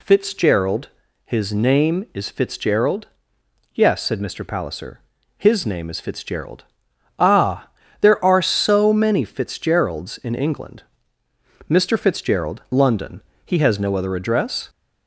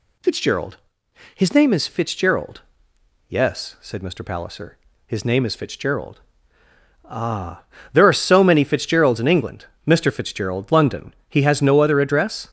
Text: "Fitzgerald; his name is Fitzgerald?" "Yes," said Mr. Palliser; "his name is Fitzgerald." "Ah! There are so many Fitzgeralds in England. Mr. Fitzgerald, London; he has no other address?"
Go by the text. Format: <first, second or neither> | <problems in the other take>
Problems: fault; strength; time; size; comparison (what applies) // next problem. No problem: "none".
neither | none